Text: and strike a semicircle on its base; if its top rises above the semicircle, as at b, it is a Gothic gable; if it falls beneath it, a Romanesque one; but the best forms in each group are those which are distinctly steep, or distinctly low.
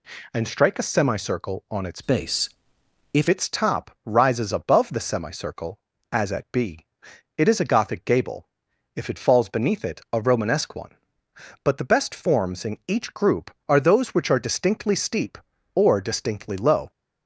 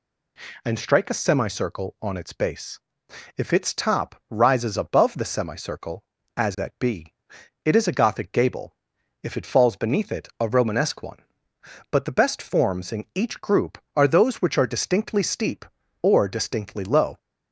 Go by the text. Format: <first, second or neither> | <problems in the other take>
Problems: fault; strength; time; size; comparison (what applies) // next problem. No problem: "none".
second | changes voice from "base" to "if"; from 2.0 to 3.2 s; 1.2 s long